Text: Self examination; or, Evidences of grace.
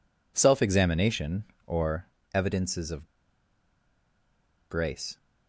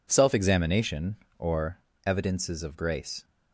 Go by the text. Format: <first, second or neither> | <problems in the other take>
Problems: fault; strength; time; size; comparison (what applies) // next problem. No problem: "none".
second | pauses between "of" and "grace"; strong; at 3.0 s; 1.6 s long